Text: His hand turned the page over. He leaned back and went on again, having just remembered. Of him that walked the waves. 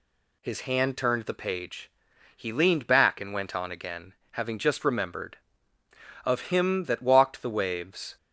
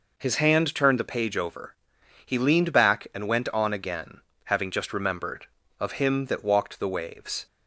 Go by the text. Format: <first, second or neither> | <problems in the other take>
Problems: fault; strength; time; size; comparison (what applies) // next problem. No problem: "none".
second | skips "over"; at 2.1 s